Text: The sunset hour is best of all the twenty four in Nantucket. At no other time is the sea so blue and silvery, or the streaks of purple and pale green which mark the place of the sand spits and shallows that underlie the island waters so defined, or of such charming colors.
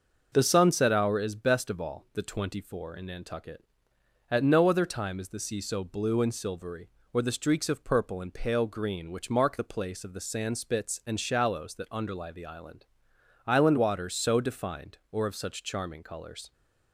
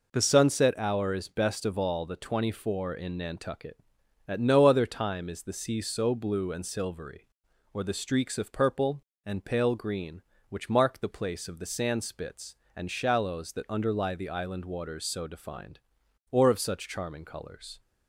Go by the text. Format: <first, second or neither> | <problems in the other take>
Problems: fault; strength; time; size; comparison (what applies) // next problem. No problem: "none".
second | starts louder than the rest; until 1.3 s; 6.5 dB // says "island" twice; at 13.4 s